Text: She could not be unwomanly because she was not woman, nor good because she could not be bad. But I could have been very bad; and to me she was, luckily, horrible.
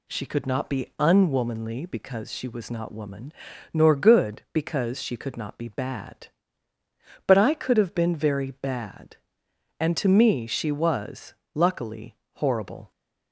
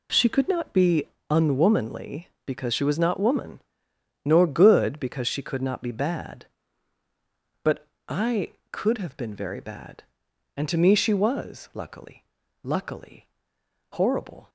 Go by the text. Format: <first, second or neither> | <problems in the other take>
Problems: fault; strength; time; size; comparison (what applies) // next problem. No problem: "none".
first | pauses between "be" and "unwomanly"; slight; at 1.0 s; 0.24 s long // pauses between "But" and "I"; slight; at 7.8 s; 0.22 s long // says "luckily" twice; at 12.6 s